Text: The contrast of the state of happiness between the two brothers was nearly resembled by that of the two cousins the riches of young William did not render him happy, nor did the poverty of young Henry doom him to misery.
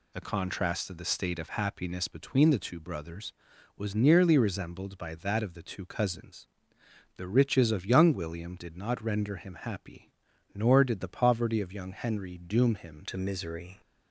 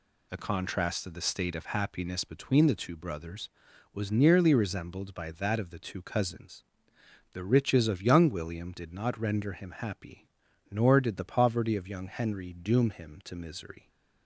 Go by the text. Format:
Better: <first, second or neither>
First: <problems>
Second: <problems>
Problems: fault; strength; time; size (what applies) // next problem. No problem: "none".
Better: second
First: pauses between "cousins" and "the"; noticeable; at 6.4 s; 0.70 s long // changes voice at "to"; from 13.0 s on; 0.8 s long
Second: pauses between "cousins" and "the"; noticeable; at 6.6 s; 0.70 s long